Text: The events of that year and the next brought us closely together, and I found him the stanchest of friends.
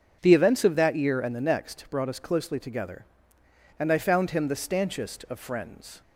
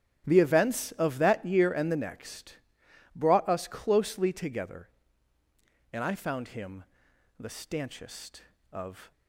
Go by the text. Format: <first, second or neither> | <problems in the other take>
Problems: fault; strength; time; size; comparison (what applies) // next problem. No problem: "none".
first | starts louder than the rest; strong; until 1.2 s; 9 dB // pauses between "next" and "brought"; noticeable; at 2.5 s; 0.58 s long // pauses between "him" and "the"; noticeable; at 6.8 s; 0.56 s long // stops before "friends"; at 9.1 s